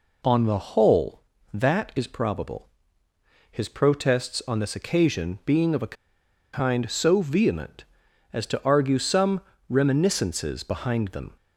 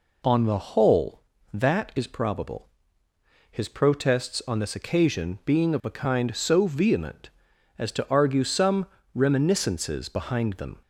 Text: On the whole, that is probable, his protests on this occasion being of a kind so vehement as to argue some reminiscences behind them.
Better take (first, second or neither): second